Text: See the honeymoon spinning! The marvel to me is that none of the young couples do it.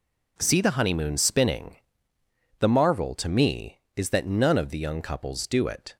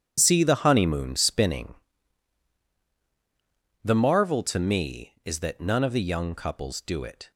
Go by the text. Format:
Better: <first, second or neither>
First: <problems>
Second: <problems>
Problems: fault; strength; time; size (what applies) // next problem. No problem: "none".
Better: first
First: none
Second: gets quieter; strong; throughout; 13 dB